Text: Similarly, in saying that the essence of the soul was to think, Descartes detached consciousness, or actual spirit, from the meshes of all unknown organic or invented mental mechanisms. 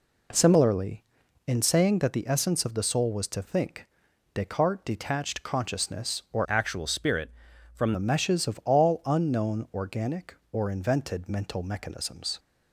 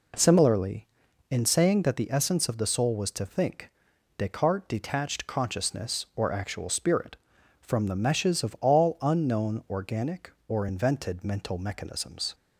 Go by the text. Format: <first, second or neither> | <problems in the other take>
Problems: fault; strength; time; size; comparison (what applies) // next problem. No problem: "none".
second | changes voice from "actual" to "from"; from 6.4 to 7.9 s; 1.5 s long